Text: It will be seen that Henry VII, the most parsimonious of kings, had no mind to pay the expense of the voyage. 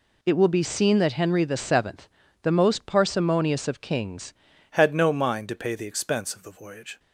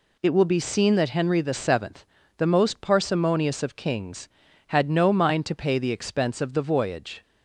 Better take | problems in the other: second | changes voice at "had"; from 4.7 s on; 2.2 s long

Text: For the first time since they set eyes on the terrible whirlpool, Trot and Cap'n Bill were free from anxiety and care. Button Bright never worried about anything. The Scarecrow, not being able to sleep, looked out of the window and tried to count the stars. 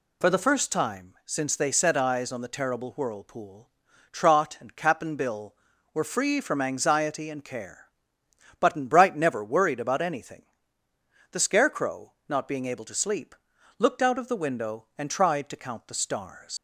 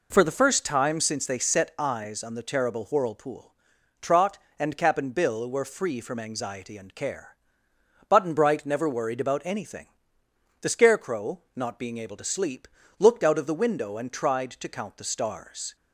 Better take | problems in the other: second | leaves "stars" unfinished; at 16.5 s; 90 ms

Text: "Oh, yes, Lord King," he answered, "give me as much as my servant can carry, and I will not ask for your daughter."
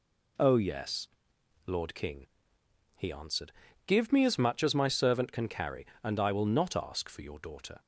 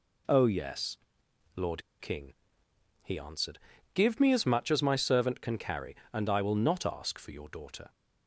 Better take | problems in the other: first | pauses between "Lord" and "King"; slight; at 1.8 s; 0.17 s long

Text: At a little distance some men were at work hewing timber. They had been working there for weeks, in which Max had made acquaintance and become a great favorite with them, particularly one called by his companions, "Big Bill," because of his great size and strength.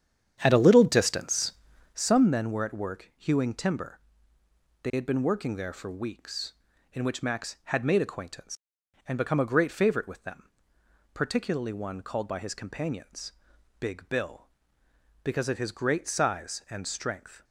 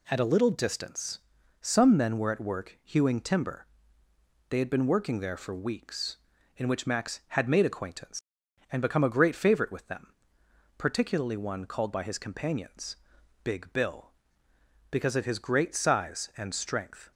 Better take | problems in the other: second | starts louder than the rest; strong; until 2.1 s; 9 dB // pauses between "distance" and "some"; at 1.5 s; 0.40 s long; also in the second

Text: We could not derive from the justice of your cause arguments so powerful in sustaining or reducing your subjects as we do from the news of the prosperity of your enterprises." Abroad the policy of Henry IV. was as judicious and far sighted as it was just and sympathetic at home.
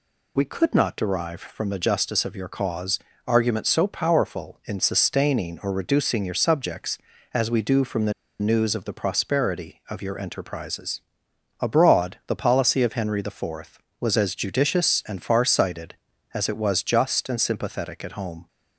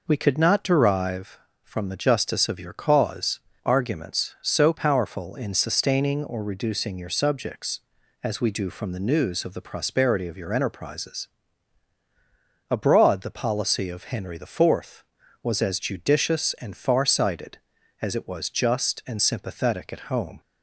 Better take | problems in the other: second | pauses between "cause" and "arguments"; slight; at 2.9 s; 0.28 s long; slight in the second // pauses between "the" and "news"; slight; at 8.1 s; 0.27 s long

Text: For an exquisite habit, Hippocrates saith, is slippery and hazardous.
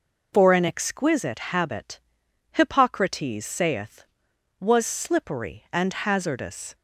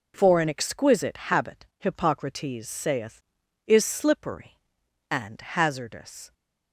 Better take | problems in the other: second | says "was" for "is"; at 4.5 s

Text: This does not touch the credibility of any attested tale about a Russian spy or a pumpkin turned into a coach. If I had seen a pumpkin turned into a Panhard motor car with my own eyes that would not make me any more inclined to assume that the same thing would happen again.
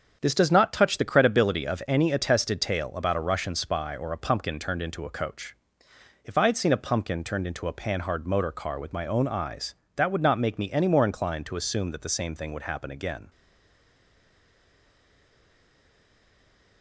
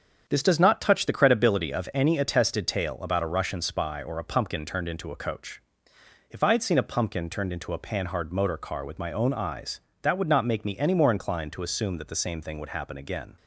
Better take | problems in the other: second | starts louder than the rest; strong; until 1.2 s; 7.5 dB; strong in the second // stays silent after the last word; strong; from 13.2 s on; 3.6 s long

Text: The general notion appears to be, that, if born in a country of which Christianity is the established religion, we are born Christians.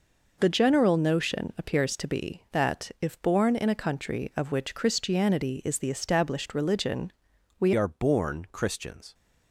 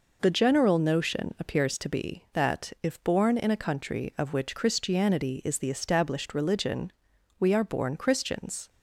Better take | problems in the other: second | changes voice at "are"; from 7.7 s on; 1.4 s long

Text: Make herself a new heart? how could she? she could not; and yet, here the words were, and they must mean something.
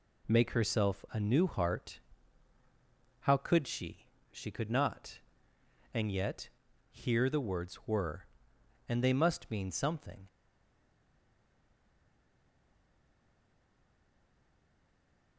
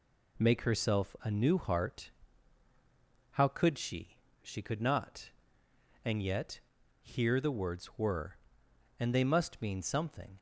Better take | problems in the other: second | stays silent after the last word; strong; from 10.2 s on; 5.1 s long

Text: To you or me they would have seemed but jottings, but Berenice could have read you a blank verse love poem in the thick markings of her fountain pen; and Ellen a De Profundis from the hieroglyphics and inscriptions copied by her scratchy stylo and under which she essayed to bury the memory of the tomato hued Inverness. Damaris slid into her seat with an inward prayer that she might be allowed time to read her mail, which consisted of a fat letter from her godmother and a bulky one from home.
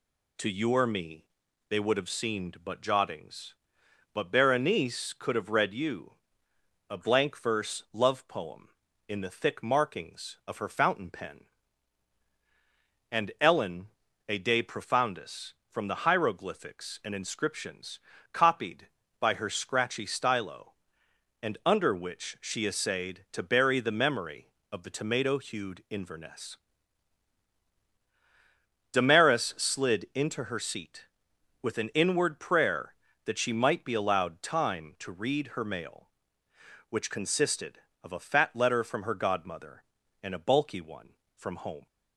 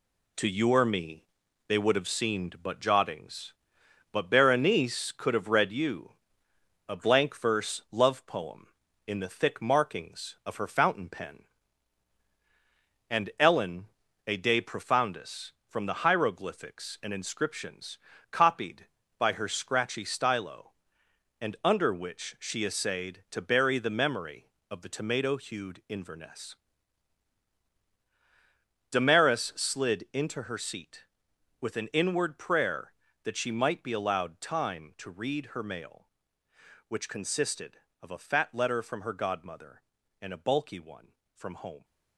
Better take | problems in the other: first | gets quieter; throughout; 7 dB // pauses between "me" and "they"; noticeable; at 1.2 s; 0.46 s long; noticeable in the first // pauses between "you" and "a"; noticeable; at 6.1 s; 0.78 s long; noticeable in the first // pauses between "Ellen" and "a"; at 13.8 s; 0.42 s long; also in the first // pauses between "inscriptions" and "copied"; slight; at 17.9 s; 0.36 s long; slight in the first

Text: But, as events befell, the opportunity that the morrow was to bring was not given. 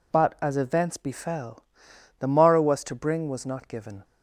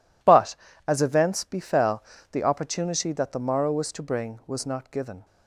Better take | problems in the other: second | skips "opportunity that the"; at 2.2 s

